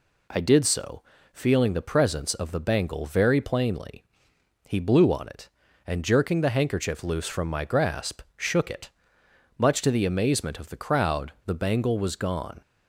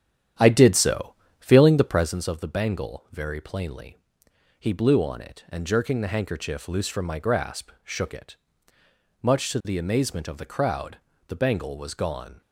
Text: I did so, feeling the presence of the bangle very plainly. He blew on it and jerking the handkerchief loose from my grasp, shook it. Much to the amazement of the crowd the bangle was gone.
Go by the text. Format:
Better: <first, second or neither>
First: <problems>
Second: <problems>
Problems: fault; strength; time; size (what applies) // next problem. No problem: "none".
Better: first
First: none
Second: starts louder than the rest; strong; until 2.2 s; 10 dB // pauses between "crowd" and "the"; slight; at 10.9 s; 0.30 s long